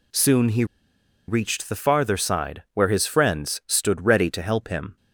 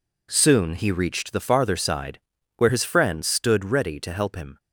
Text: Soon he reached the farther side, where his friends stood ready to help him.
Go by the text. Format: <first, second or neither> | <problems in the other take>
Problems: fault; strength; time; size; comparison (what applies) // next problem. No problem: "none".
second | pauses between "he" and "reached"; noticeable; at 0.6 s; 0.62 s long